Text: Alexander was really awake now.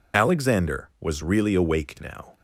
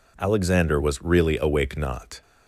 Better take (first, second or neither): first